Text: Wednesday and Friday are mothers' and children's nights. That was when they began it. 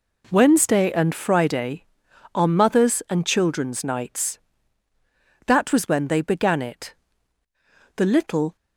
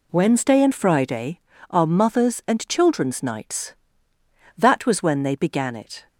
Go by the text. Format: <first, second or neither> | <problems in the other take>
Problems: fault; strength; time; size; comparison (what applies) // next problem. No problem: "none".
second | goes on to say "The little"; from 7.9 s on; 0.58 s long